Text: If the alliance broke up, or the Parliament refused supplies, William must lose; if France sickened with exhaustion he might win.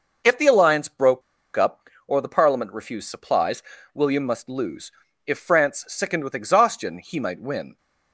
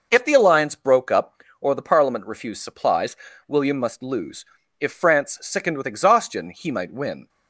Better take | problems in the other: second | pauses between "broke" and "up"; slight; at 1.2 s; 0.35 s long

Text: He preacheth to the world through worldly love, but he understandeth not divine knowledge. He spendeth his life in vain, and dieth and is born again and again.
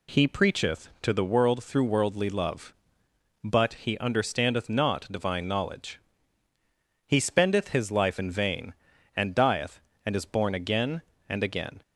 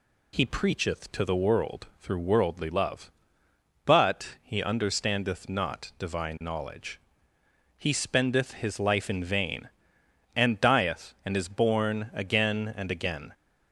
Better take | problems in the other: neither | none

